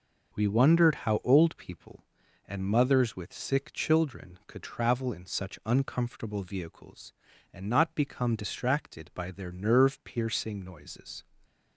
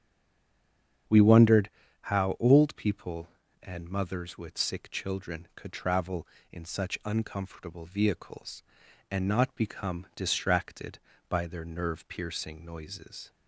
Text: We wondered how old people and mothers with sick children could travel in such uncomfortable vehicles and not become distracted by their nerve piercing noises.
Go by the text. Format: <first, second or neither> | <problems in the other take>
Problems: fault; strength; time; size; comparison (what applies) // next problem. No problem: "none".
first | stays silent before the first word; until 1.0 s; 1.0 s long // starts louder than the rest; strong; until 2.4 s; 7.5 dB // pauses between "wondered" and "how"; slight; at 1.6 s; 0.32 s long